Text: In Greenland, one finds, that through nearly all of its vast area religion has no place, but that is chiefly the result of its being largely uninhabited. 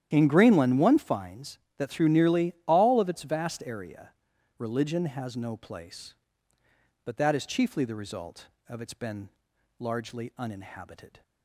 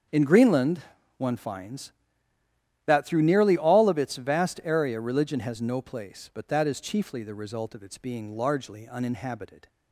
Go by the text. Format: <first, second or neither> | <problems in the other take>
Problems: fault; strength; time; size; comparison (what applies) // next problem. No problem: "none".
second | starts louder than the rest; strong; until 1.1 s; 11 dB; strong in the second // pauses between "nearly" and "all"; slight; at 2.5 s; 0.16 s long // pauses between "area" and "religion"; noticeable; at 4.0 s; 0.48 s long // says "been" for "being"; at 8.9 s